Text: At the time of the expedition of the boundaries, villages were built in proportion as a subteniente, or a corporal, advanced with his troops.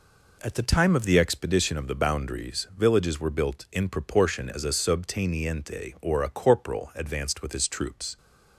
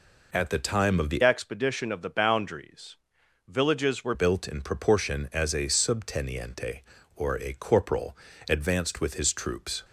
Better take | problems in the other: first | changes voice from "expedition" to "were"; from 1.2 to 4.1 s; 2.9 s long

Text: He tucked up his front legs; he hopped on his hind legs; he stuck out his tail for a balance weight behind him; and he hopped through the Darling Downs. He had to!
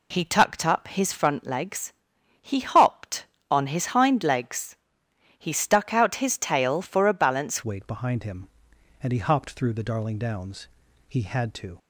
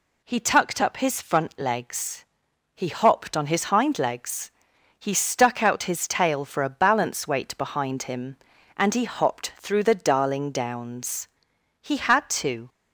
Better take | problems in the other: second | changes voice at "weight"; from 7.6 s on; 4.1 s long

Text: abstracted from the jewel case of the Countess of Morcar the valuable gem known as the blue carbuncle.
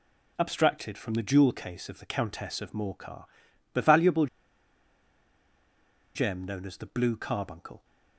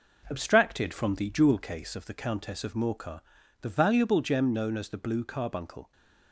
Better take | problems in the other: second | pauses between "Morcar" and "the"; noticeable; at 3.2 s; 0.48 s long; also in the second // pauses between "valuable" and "gem"; strong; at 4.2 s; 1.8 s long

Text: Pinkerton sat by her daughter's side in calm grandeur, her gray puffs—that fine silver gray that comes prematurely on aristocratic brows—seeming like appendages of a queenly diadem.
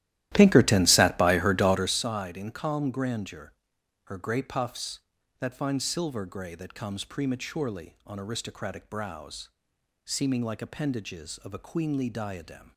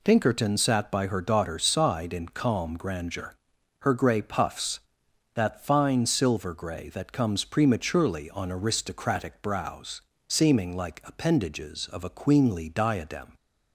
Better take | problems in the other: second | starts louder than the rest; strong; until 2.1 s; 14 dB

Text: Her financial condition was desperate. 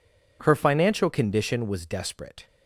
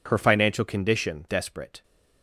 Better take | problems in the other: first | skips "was"; at 1.2 s

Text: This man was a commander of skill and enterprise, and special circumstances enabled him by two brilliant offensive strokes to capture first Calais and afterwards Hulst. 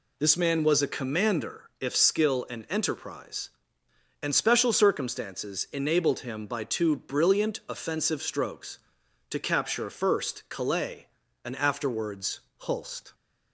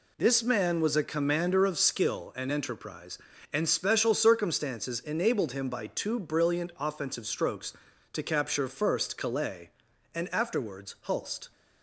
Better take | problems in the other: second | says "if" for "of"; at 1.8 s // pauses between "afterwards" and "Hulst"; slight; at 12.4 s; 0.20 s long

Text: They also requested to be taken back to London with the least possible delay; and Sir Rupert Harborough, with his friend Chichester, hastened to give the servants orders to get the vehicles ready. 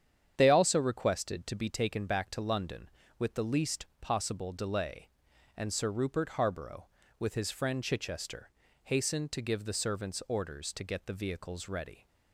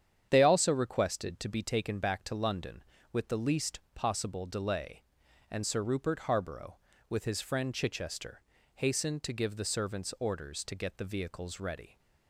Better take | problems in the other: neither | starts louder than the rest; strong; the same in both // pauses between "least" and "possible"; slight; the same in both

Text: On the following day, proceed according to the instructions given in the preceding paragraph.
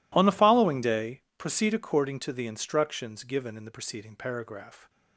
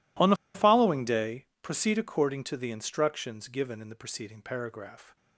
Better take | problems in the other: first | pauses between "the" and "following"; slight; at 0.3 s; 0.18 s long

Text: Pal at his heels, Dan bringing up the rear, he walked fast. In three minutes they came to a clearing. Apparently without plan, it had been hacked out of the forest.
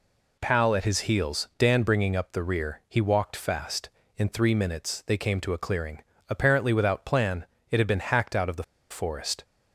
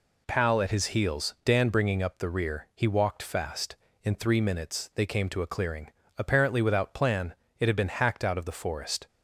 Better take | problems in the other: second | pauses between "the" and "forest"; slight; at 8.6 s; 0.26 s long

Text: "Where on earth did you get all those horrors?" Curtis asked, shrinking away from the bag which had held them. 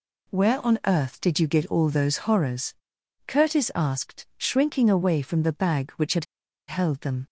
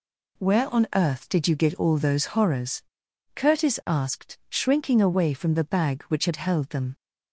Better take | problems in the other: second | pauses between "had" and "held"; at 6.2 s; 0.42 s long

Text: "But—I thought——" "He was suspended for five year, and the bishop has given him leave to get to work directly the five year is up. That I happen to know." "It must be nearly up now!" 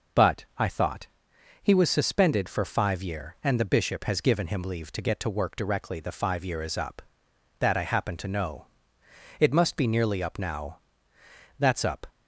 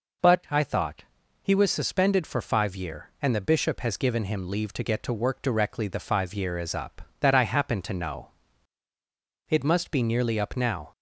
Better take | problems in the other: second | goes on to say "That's up"; slight; from 11.5 s on; 0.48 s long

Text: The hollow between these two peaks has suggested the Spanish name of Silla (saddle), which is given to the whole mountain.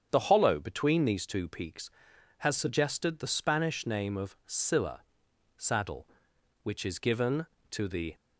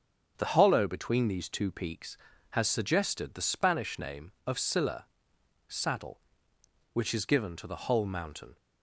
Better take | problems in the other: second | starts louder than the rest; strong; until 1.1 s; 8 dB; strong in the second // stops before "whole mountain"; at 8.1 s

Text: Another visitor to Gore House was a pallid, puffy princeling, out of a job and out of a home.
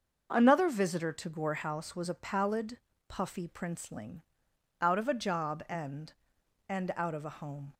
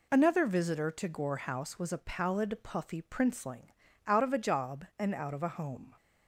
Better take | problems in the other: second | starts louder than the rest; until 1.3 s; 6 dB // says "and" twice; at 6.6 s

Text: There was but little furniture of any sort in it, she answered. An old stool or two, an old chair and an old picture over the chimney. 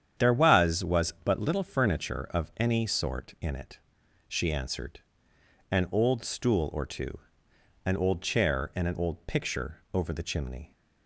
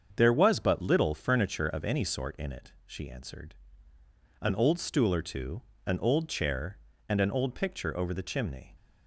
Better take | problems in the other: second | starts louder than the rest; strong; until 1.3 s; 9 dB; also in the second // says "was" twice; at 0.8 s

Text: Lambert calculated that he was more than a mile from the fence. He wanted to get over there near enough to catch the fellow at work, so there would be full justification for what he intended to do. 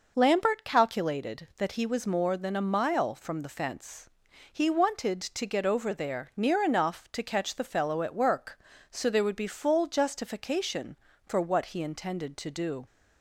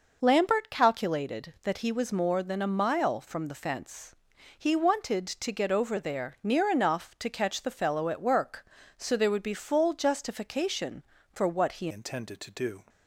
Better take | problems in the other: first | changes voice at "intended"; from 11.9 s on; 0.9 s long

